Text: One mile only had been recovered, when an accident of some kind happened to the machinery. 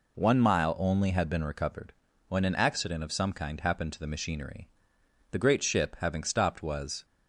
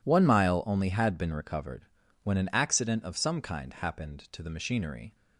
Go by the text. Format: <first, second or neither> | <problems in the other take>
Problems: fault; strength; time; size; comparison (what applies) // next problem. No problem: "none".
second | goes on to say "The great ship having stopped was"; strong; from 5.3 s on; 1.7 s long